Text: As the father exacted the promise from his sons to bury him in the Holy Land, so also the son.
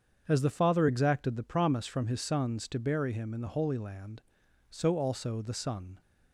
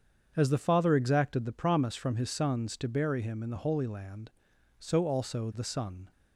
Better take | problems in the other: neither | starts louder than the rest; strong; the same in both

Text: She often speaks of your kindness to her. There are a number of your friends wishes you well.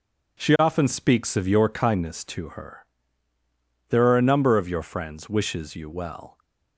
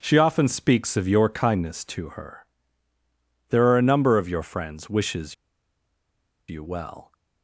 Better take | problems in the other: first | pauses between "wishes" and "you"; at 5.3 s; 1.1 s long

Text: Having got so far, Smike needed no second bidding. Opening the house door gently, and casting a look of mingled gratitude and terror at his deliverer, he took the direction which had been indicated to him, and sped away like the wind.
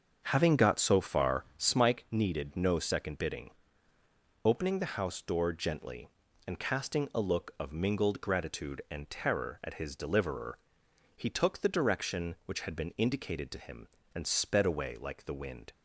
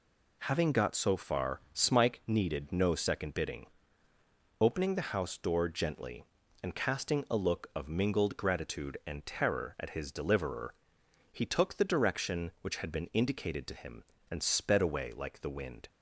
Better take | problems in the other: second | starts louder than the rest; until 1.7 s; 7 dB

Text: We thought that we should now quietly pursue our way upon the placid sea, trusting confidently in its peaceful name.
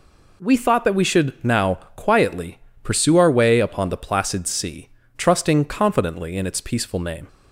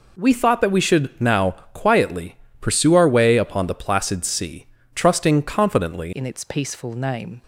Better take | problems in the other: first | pauses between "now" and "quietly"; slight; at 1.5 s; 0.24 s long; slight in the first // pauses between "quietly" and "pursue"; slight; at 2.3 s; 0.22 s long; slight in the first // changes voice at "in"; from 6.1 s on; 1.3 s long

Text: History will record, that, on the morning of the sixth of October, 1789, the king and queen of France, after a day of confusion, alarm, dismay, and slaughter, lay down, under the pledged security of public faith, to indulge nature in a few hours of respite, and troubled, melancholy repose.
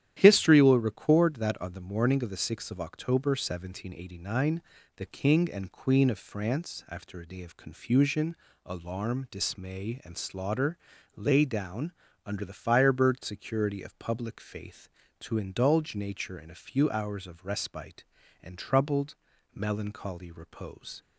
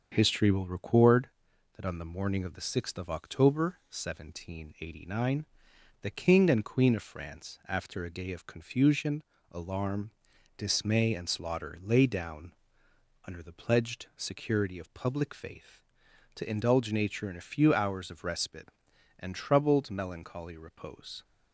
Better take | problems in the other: second | starts louder than the rest; strong; until 1.2 s; 11 dB; also in the second // says "firebird" for "pledged"; at 12.5 s

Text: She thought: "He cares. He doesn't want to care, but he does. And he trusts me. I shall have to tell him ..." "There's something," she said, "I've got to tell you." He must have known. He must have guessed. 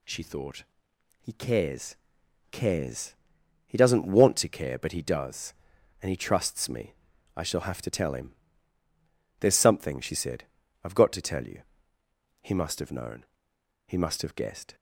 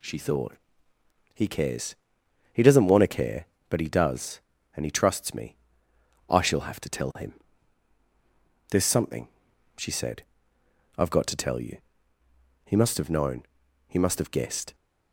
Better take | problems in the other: second | says "cares" twice; at 2.5 s

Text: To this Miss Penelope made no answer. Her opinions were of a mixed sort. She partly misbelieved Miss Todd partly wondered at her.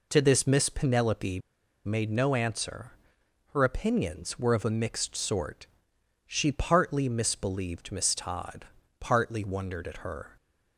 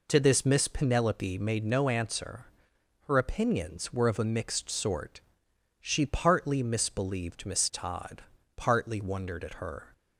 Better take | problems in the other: second | pauses between "Penelope" and "made"; noticeable; at 1.3 s; 0.47 s long // pauses between "Todd" and "partly"; slight; at 8.6 s; 0.34 s long; slight in the second

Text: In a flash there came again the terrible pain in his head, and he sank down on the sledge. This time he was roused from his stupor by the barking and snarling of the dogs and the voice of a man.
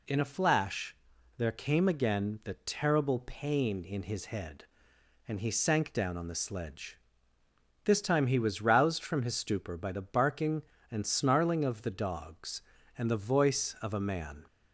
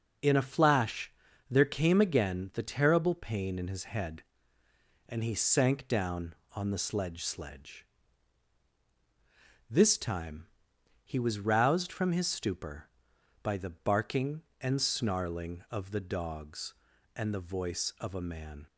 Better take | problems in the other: first | pauses between "flash" and "there"; at 1.1 s; 0.38 s long; also in the first // says "sledge" twice; at 7.2 s // pauses between "time" and "he"; noticeable; at 10.4 s; 0.56 s long

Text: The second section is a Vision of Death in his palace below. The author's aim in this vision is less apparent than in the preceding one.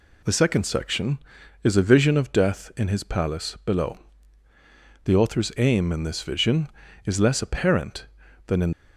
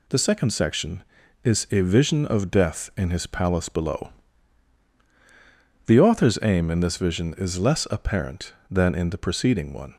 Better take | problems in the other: second | stops before "the preceding one"; at 8.7 s

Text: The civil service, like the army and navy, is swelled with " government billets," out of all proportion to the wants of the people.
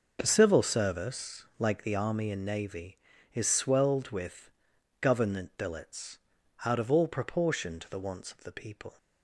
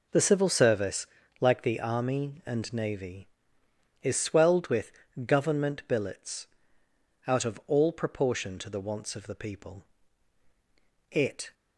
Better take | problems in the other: first | goes on to say "It"; slight; from 11.1 s on; 0.42 s long

